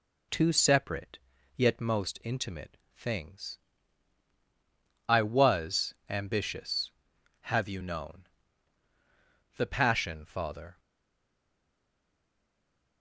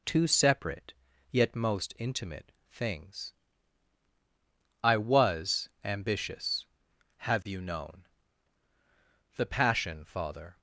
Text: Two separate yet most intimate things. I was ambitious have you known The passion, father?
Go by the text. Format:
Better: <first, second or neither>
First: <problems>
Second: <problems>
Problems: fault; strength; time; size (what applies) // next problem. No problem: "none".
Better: second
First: pauses between "separate" and "yet"; at 1.1 s; 0.40 s long // pauses between "intimate" and "things"; slight; at 2.7 s; 0.18 s long // pauses between "known" and "The"; strong; at 8.2 s; 1.2 s long // stays silent after the last word; from 10.7 s on; 2.3 s long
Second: pauses between "separate" and "yet"; at 0.9 s; 0.40 s long // pauses between "intimate" and "things"; slight; at 2.5 s; 0.18 s long // pauses between "known" and "The"; strong; at 8.0 s; 1.2 s long